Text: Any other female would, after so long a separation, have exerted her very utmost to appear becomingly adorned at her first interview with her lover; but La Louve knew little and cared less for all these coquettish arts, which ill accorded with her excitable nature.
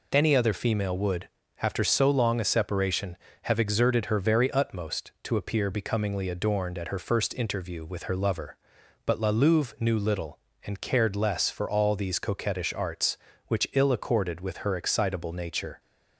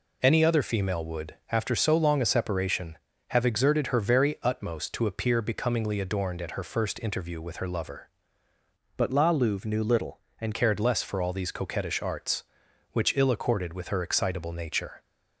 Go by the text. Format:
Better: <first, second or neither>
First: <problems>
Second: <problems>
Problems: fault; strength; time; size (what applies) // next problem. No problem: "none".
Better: first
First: none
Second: changes voice from "but" to "and"; from 8.9 to 10.5 s; 1.6 s long